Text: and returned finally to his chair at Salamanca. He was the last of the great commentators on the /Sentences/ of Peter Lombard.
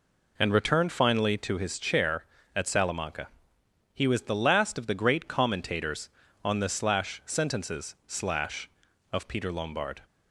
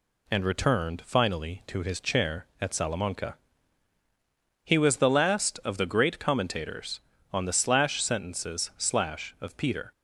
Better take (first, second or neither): first